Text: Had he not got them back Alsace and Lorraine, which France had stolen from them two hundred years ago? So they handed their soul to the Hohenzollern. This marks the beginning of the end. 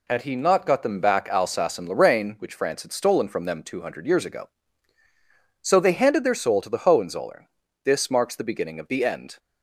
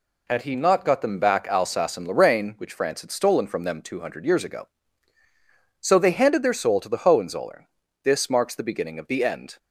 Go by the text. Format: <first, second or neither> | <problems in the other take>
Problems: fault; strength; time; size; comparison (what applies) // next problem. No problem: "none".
neither | none